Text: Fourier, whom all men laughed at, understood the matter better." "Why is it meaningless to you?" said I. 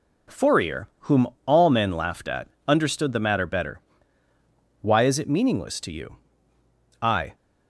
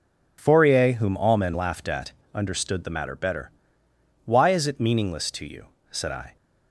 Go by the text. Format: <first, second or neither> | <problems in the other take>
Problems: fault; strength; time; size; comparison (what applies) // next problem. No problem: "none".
second | pauses between "whom" and "all"; slight; at 1.2 s; 0.20 s long // skips "said"; at 6.5 s